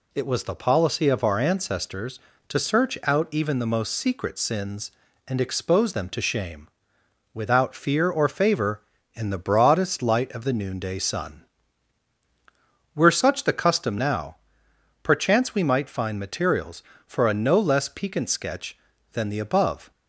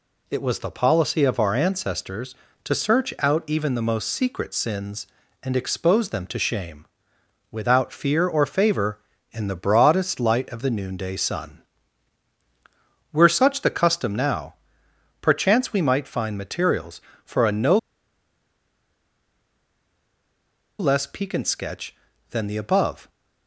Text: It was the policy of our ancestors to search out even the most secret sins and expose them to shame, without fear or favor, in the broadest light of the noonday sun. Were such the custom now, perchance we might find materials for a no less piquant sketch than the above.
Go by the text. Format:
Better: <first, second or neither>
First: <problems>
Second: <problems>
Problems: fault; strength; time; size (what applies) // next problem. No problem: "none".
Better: first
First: none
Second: pauses between "no" and "less"; strong; at 17.7 s; 3.0 s long